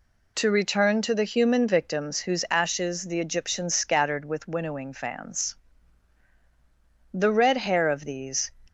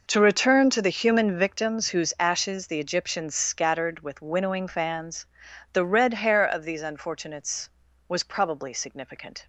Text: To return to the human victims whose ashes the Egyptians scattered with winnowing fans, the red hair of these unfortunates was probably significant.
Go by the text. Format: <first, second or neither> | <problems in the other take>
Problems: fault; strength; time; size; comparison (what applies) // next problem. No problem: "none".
second | stops before "unfortunates was probably significant"; at 8.6 s